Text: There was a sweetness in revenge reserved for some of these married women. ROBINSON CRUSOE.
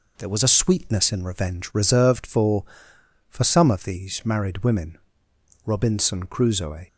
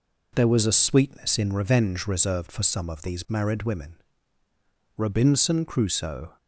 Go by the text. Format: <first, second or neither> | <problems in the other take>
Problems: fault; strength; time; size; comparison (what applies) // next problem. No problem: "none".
second | says "for" twice; at 3.2 s